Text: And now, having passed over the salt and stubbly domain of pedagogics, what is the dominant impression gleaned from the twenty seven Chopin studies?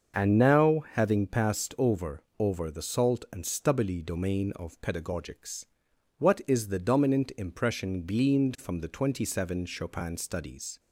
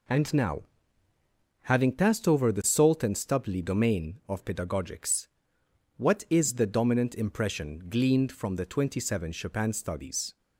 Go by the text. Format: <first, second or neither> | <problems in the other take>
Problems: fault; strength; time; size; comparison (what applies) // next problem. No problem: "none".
second | starts louder than the rest; until 1.2 s; 6.5 dB // says "over" twice; at 2.3 s